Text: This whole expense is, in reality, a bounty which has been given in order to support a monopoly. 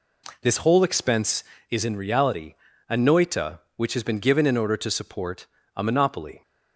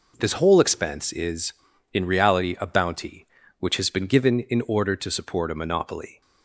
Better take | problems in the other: second | says "noita" for "bounty"; at 2.9 s // pauses between "support" and "a"; slight; at 5.4 s; 0.32 s long

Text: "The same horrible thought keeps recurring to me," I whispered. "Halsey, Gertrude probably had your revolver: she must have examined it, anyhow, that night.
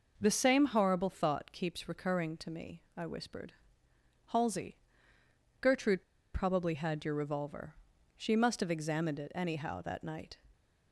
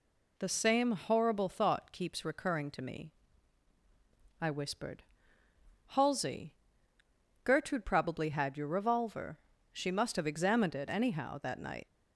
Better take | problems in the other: second | pauses between "Gertrude" and "probably"; slight; at 6.0 s; 0.30 s long

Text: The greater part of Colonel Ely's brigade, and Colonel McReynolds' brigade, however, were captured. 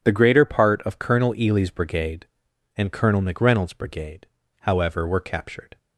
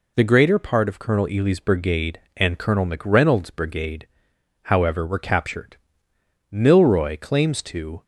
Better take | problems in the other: first | goes on to say "Milroy claims to"; from 6.5 s on; 1.5 s long

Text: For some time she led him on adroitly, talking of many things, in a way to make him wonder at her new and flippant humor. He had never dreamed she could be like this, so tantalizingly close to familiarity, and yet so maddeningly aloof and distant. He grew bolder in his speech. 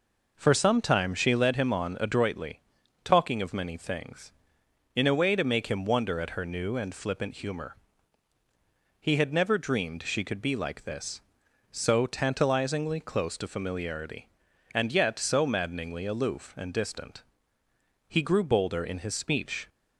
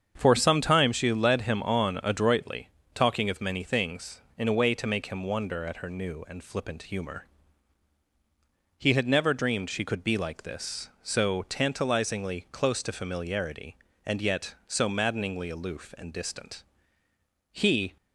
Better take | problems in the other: first | starts louder than the rest; strong; until 1.1 s; 7.5 dB // stops before "grew bolder in his speech"; at 17.9 s

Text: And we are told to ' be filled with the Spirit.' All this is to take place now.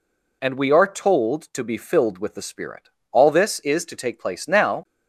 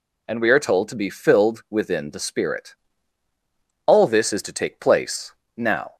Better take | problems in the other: first | says "within" for "with"; at 1.6 s // pauses between "place" and "now"; slight; at 5.3 s; 0.24 s long

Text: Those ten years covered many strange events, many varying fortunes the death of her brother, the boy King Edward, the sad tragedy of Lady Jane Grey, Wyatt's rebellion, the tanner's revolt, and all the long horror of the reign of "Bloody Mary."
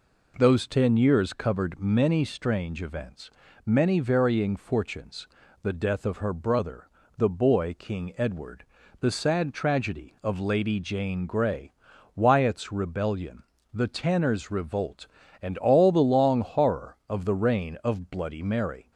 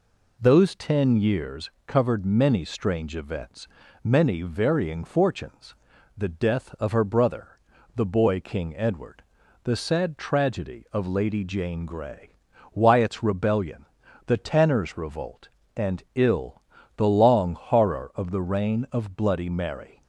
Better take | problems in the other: first | pauses between "years" and "covered"; slight; at 1.6 s; 0.18 s long // pauses between "fortunes" and "the"; at 5.7 s; 0.42 s long; slight in the first // says "ill" for "all"; at 16.1 s

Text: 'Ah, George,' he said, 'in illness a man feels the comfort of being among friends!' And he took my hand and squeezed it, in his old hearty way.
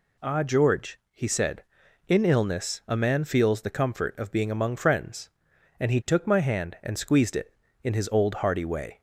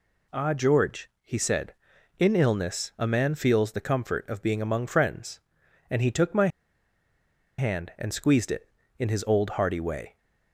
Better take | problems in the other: first | pauses between "my" and "hand"; at 6.4 s; 1.1 s long

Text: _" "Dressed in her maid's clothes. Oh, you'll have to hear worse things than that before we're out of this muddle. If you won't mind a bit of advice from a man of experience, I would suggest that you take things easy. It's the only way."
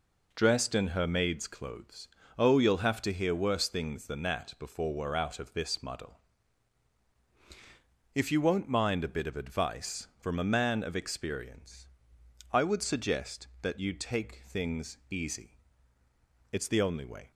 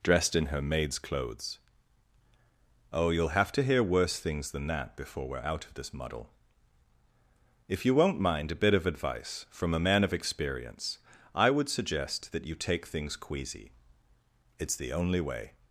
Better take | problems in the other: first | says "queasy" for "easy"; at 13.1 s

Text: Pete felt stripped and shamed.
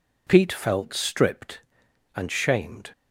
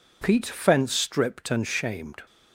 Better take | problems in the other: first | says "fence" for "felt"; at 0.4 s

